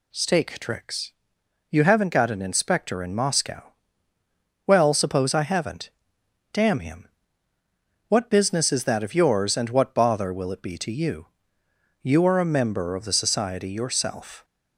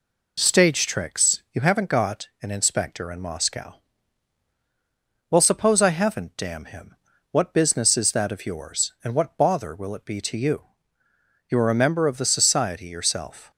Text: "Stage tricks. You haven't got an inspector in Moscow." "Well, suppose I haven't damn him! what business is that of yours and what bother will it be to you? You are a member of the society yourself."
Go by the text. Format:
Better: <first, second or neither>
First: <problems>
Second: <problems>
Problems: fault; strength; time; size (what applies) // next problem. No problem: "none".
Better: second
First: says "Stake" for "Stage"; at 0.1 s // pauses between "haven't" and "damn"; noticeable; at 5.9 s; 0.62 s long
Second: none